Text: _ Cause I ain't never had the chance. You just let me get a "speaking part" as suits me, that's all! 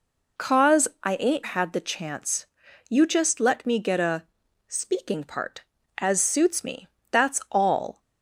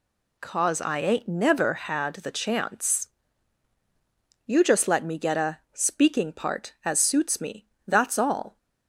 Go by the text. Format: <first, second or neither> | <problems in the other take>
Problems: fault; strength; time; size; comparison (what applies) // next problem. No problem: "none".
second | skips "never"; at 1.4 s // pauses between "a" and "speaking"; at 4.2 s; 0.42 s long